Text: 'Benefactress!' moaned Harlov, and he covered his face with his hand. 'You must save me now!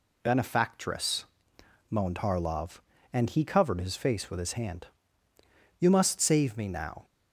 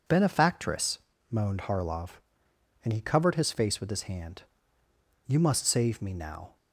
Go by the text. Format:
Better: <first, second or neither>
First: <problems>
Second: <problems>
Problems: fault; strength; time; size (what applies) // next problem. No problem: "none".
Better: neither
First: none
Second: none